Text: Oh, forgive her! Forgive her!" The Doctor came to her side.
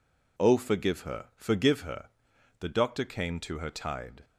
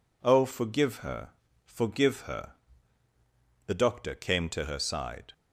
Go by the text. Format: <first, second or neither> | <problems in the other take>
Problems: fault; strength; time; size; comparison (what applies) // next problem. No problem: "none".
second | says "tide" for "side"; at 3.7 s